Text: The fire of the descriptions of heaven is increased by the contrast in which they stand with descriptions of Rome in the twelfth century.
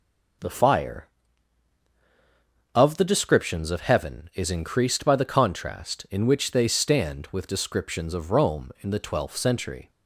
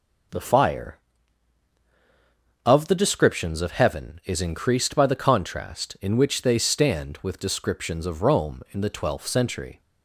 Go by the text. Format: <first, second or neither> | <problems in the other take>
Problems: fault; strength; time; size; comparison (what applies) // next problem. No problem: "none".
neither | none